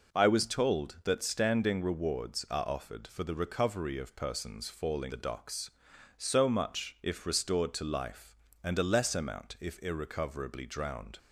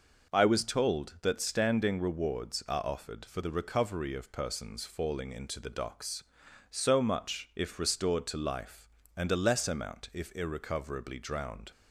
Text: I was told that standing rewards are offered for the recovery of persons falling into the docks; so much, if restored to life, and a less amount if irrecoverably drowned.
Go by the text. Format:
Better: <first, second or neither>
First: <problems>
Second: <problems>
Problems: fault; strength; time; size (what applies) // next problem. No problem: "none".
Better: second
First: skips "into"; at 5.1 s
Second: none